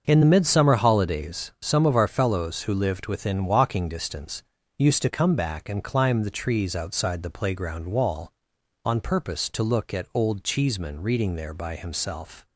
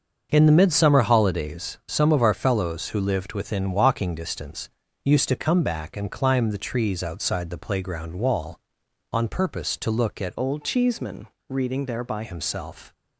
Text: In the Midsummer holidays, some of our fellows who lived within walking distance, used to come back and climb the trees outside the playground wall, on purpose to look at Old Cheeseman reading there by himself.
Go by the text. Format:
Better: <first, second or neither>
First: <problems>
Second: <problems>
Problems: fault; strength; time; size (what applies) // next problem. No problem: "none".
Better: first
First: starts louder than the rest; until 1.0 s; 6.5 dB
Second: starts louder than the rest; until 1.3 s; 6.5 dB // changes voice from "Old" to "by"; from 10.3 to 12.2 s; 1.9 s long // pauses between "Cheeseman" and "reading"; slight; at 11.2 s; 0.22 s long